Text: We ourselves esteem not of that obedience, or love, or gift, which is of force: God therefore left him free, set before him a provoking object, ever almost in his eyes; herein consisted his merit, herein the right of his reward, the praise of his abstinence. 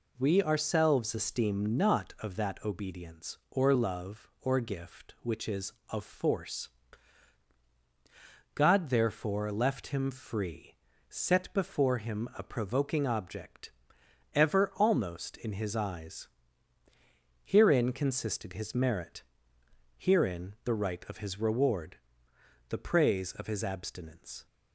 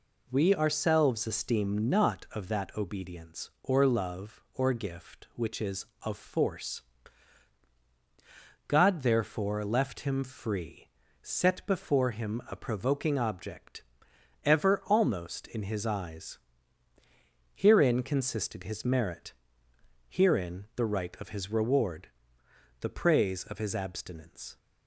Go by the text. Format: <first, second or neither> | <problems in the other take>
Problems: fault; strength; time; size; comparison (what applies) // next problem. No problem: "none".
neither | none